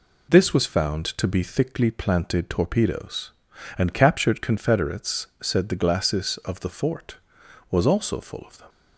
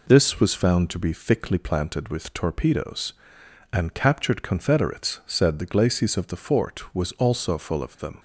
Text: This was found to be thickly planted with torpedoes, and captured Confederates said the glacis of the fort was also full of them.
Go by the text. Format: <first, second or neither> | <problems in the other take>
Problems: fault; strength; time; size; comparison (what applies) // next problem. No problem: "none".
second | skips "with"; at 2.5 s // pauses between "Confederates" and "said"; slight; at 5.2 s; 0.16 s long